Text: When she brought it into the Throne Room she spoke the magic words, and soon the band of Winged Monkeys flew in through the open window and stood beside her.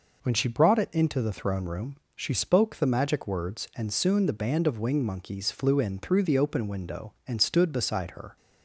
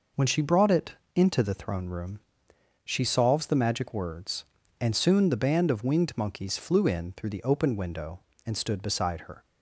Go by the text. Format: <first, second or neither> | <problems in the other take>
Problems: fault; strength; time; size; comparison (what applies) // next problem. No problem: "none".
first | pauses between "it" and "into"; slight; at 0.9 s; 0.20 s long // pauses between "Room" and "she"; noticeable; at 2.1 s; 0.64 s long; slight in the first // says "solves" for "spoke"; at 3.0 s